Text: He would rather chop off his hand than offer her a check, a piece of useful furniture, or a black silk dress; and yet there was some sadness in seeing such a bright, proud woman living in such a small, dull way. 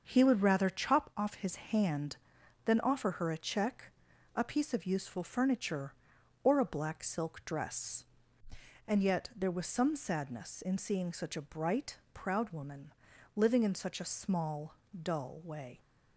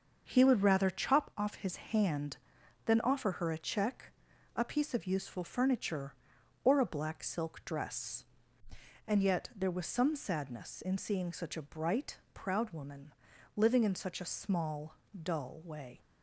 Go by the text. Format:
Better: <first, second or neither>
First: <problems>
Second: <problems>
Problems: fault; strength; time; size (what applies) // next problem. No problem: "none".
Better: neither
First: starts louder than the rest; until 1.0 s; 6.5 dB // pauses between "woman" and "living"; at 12.9 s; 0.44 s long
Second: starts louder than the rest; until 1.2 s; 6.5 dB // pauses between "woman" and "living"; at 13.1 s; 0.44 s long